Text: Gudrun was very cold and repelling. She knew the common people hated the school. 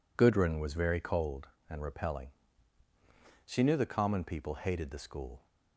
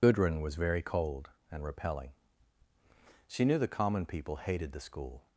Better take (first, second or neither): first